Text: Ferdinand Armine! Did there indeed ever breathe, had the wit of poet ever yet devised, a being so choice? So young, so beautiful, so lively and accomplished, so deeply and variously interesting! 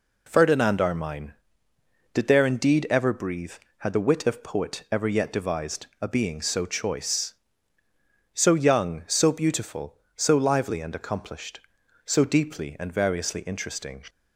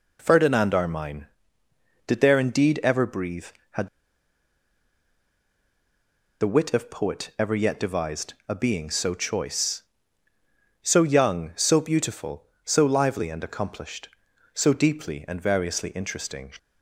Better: first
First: none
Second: pauses between "had" and "the"; strong; at 3.8 s; 2.5 s long

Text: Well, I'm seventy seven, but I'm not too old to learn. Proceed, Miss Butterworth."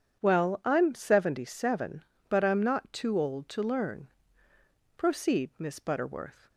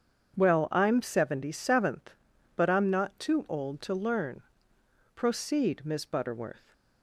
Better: first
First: none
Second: starts louder than the rest; strong; until 1.4 s; 7 dB // says "seventh" for "seven"; at 1.5 s

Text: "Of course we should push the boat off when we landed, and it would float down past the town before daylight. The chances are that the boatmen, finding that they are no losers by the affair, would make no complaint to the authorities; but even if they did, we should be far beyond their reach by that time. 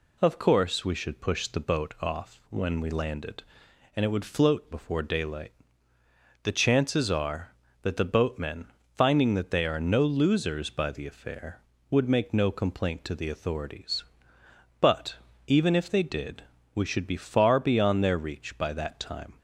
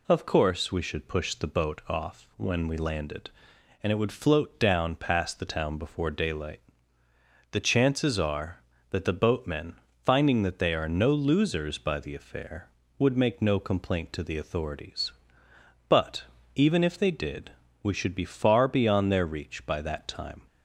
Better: second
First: skips "down past the town"; at 4.7 s // pauses between "but" and "even"; slight; at 15.1 s; 0.28 s long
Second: pauses between "but" and "even"; slight; at 16.2 s; 0.28 s long

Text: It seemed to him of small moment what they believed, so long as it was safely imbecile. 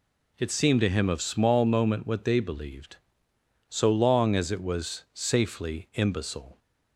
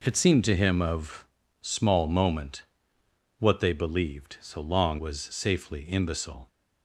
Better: first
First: none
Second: pauses between "of" and "small"; slight; at 1.2 s; 0.36 s long // pauses between "moment" and "what"; noticeable; at 2.6 s; 0.76 s long // skips "as it"; at 4.9 s

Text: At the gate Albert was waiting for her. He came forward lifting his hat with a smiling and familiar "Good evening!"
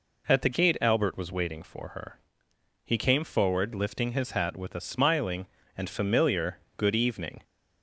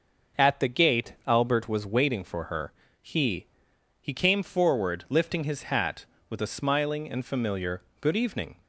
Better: first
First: pauses between "familiar" and "Good"; slight; at 6.5 s; 0.22 s long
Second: says "He" twice; at 4.0 s // pauses between "familiar" and "Good"; slight; at 7.8 s; 0.16 s long

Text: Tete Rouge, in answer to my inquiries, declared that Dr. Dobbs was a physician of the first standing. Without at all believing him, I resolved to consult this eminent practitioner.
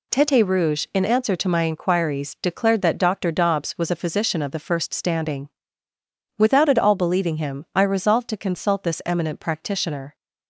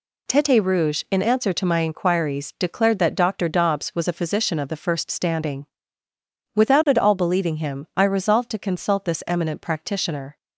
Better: neither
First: none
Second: none

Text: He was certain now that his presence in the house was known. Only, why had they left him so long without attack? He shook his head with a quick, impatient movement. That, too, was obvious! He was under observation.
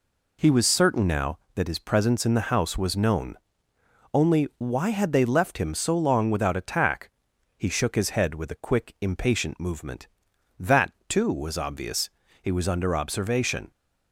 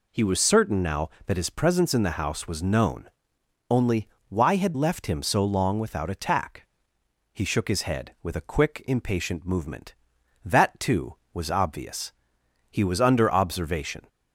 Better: first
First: none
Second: skips "they"; at 4.7 s

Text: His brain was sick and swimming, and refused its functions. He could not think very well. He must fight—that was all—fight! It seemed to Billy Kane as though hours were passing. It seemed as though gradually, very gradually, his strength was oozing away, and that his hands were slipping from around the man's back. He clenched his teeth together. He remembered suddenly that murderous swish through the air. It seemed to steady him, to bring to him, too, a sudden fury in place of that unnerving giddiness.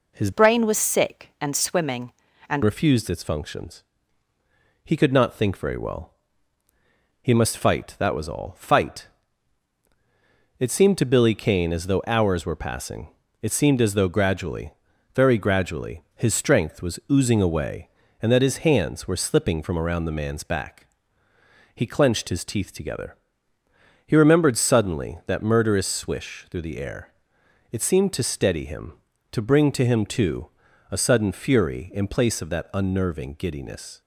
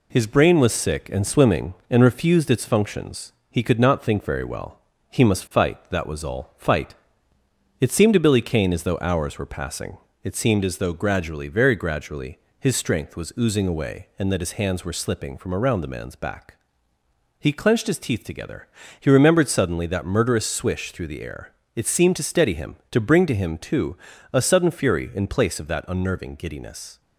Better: second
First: changes voice from "brain" to "and"; from 0.3 to 2.6 s; 2.3 s long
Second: none

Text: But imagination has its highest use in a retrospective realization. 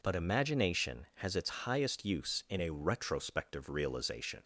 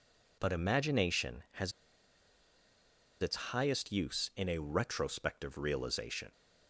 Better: first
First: none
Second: pauses between "has" and "its"; strong; at 1.7 s; 1.4 s long

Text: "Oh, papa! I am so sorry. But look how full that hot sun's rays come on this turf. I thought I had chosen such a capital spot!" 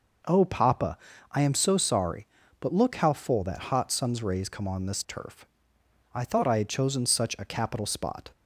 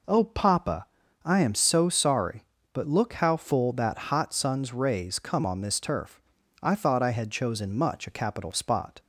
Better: first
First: none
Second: says "much" for "such"; at 7.7 s

